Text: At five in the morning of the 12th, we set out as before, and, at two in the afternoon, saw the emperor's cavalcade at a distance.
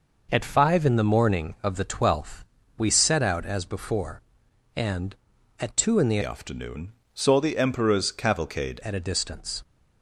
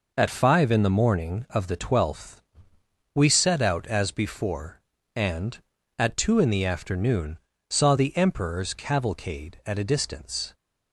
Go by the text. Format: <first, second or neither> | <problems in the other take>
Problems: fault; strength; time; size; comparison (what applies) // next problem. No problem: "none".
second | changes voice from "afternoon" to "cavalcade"; from 6.2 to 8.7 s; 2.5 s long